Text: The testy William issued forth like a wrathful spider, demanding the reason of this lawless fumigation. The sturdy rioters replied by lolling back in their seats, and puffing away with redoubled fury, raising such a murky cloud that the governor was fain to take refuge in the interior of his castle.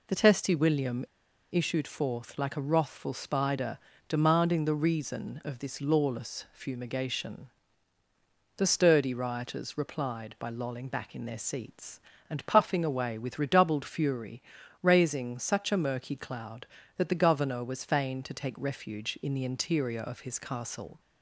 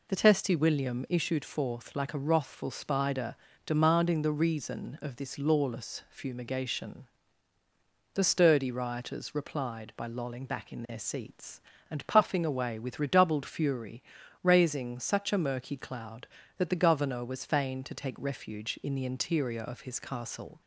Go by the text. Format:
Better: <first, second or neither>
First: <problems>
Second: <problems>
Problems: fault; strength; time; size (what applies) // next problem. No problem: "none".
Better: second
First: pauses between "William" and "issued"; noticeable; at 1.0 s; 0.46 s long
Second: none